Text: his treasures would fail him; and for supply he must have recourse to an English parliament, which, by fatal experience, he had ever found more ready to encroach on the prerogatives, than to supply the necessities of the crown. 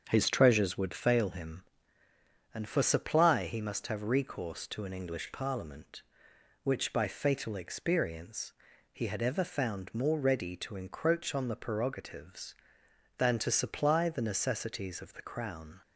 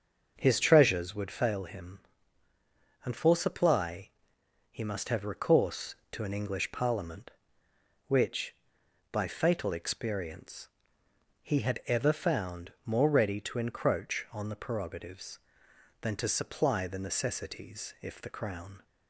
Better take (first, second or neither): first